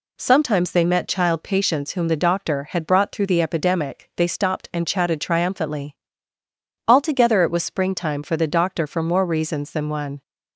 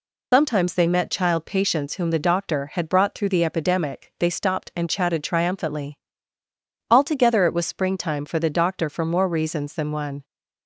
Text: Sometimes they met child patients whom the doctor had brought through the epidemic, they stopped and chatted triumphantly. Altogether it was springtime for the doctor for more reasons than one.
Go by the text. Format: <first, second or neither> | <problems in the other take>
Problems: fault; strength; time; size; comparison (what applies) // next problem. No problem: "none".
first | loses the start of "Sometimes"; at 0.3 s; 120 ms